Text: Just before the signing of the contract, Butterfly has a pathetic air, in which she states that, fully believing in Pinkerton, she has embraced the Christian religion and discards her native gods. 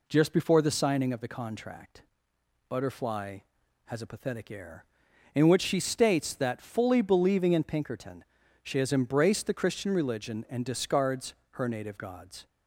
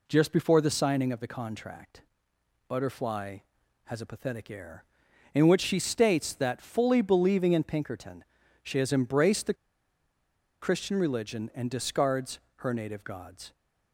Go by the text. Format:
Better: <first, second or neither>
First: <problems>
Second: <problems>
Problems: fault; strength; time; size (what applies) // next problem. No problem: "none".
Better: first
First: pauses between "discards" and "her"; slight; at 11.3 s; 0.18 s long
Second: pauses between "the" and "Christian"; at 9.5 s; 1.0 s long // pauses between "discards" and "her"; slight; at 12.3 s; 0.18 s long